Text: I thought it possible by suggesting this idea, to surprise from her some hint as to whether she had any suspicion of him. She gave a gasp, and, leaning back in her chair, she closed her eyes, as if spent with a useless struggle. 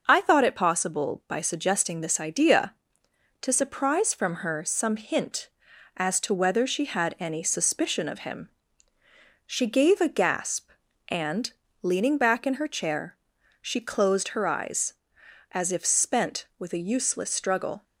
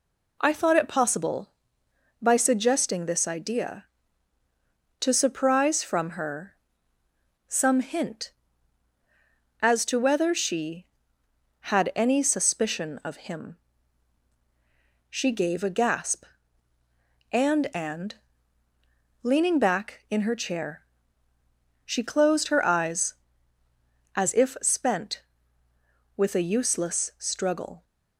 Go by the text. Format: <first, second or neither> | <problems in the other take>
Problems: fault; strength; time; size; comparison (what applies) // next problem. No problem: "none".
first | pauses between "her" and "some"; noticeable; at 6.5 s; 0.94 s long // says "and" twice; at 17.7 s